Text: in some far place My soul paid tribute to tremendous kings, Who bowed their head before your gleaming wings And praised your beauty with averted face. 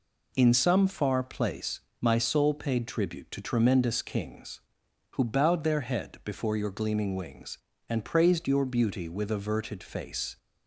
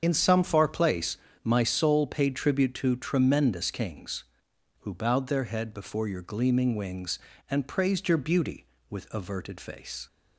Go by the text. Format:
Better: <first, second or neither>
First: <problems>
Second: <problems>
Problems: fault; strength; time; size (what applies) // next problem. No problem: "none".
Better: first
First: pauses between "place" and "My"; slight; at 1.8 s; 0.18 s long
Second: loses the start of "in"; at 0.0 s; 55 ms // starts louder than the rest; strong; until 1.0 s; 7 dB // pauses between "place" and "My"; slight; at 1.1 s; 0.26 s long